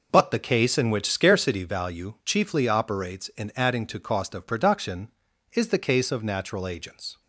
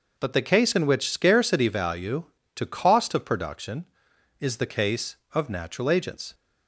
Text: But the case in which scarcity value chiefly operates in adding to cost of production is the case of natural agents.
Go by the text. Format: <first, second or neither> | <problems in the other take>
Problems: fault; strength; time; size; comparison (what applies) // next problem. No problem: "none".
first | skips "chiefly operates in adding"; at 2.3 s